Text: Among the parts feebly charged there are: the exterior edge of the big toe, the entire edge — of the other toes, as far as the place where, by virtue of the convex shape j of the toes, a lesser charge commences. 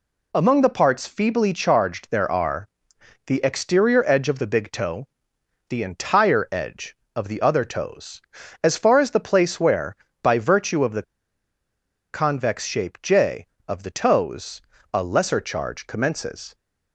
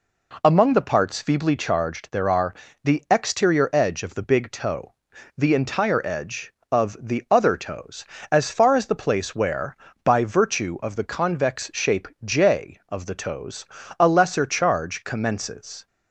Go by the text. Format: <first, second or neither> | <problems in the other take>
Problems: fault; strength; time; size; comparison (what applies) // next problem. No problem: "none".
second | pauses between "the" and "convex"; at 11.0 s; 1.0 s long